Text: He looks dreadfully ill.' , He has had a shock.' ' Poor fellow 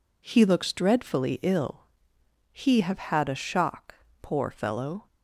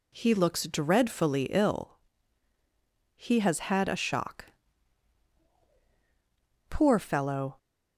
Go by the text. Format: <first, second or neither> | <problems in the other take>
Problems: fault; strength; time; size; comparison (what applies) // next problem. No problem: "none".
second | says "have" for "has"; at 2.7 s